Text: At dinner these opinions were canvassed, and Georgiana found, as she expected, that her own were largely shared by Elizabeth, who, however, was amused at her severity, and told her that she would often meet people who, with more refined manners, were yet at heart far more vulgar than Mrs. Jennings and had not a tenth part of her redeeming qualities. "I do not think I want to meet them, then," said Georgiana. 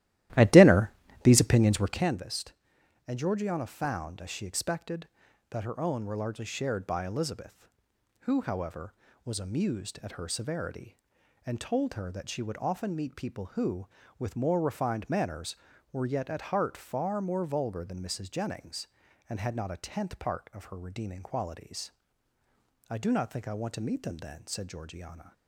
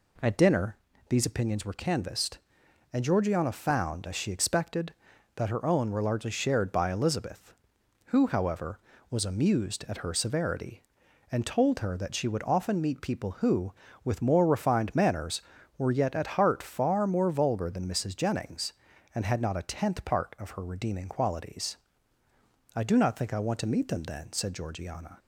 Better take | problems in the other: second | starts louder than the rest; strong; until 2.2 s; 14.5 dB // pauses between "dinner" and "these"; slight; at 0.9 s; 0.32 s long; slight in the second

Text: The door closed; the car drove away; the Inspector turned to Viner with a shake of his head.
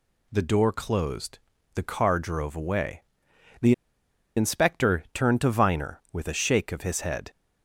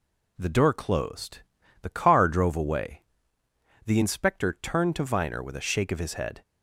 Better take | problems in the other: second | pauses between "the" and "Inspector"; noticeable; at 3.7 s; 0.64 s long

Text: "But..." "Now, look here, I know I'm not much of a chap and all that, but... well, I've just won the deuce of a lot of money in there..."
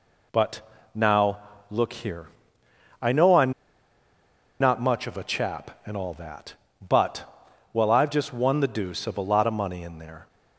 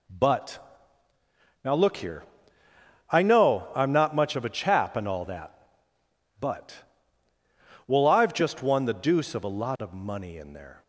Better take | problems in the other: second | pauses between "I'm" and "not"; at 3.5 s; 1.0 s long

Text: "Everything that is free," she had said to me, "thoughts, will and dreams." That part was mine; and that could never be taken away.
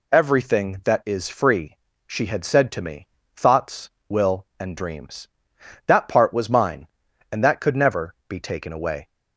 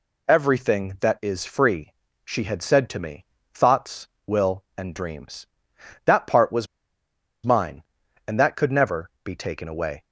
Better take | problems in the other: first | pauses between "was" and "mine"; noticeable; at 6.6 s; 0.77 s long

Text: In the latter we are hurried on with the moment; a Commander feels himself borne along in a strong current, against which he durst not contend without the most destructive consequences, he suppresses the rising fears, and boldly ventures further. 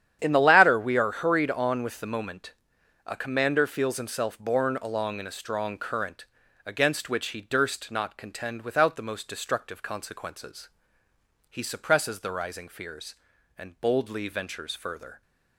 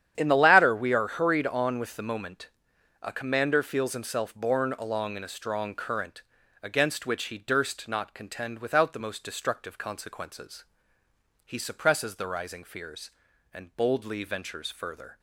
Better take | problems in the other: neither | starts louder than the rest; strong; the same in both

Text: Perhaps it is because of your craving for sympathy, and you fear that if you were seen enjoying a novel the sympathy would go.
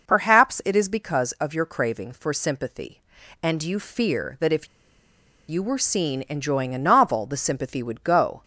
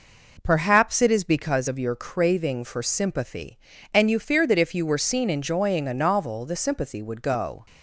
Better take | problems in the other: second | pauses between "if" and "you"; noticeable; at 4.6 s; 0.81 s long

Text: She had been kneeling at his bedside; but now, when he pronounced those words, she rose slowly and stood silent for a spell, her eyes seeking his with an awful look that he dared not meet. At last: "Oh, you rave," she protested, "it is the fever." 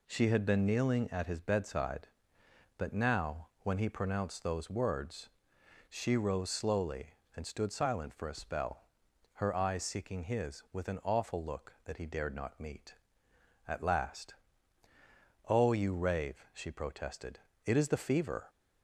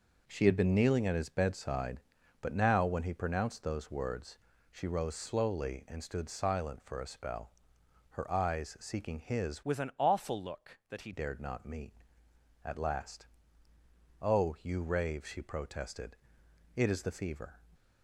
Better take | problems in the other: first | changes voice from "with" to "he"; from 9.6 to 11.1 s; 1.5 s long

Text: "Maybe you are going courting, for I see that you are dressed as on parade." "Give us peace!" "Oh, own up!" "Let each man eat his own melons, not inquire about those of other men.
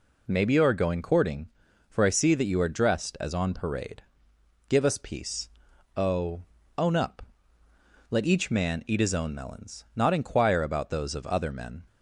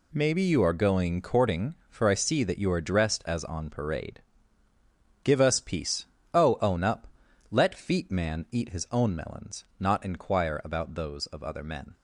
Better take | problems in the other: first | says "feet" for "each"; at 7.7 s

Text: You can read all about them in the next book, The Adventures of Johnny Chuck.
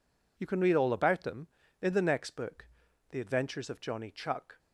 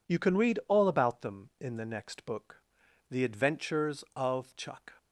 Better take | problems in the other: first | skips "Johnny"; at 4.5 s

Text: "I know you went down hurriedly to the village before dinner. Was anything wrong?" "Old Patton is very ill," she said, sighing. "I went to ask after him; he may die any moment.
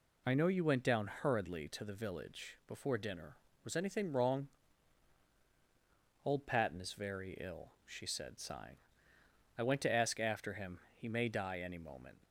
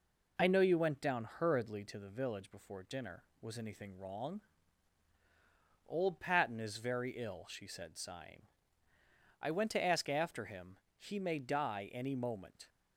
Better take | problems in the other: neither | none

